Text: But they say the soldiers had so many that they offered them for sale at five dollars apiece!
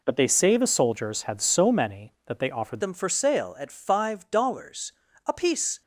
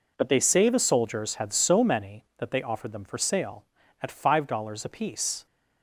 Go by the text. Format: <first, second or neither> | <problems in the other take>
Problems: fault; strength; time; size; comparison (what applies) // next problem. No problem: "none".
second | changes voice at "them"; from 2.8 s on; 3.0 s long // pauses between "dollars" and "apiece"; slight; at 4.9 s; 0.34 s long